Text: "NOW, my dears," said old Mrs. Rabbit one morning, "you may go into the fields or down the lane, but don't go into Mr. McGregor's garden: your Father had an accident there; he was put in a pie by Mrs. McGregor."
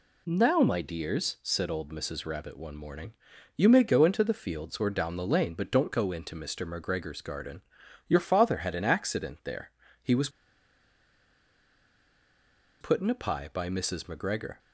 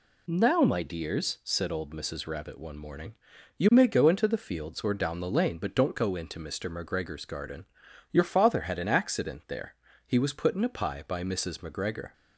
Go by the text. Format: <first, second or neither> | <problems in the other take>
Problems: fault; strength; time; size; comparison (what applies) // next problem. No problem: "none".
second | pauses between "was" and "put"; strong; at 10.2 s; 2.5 s long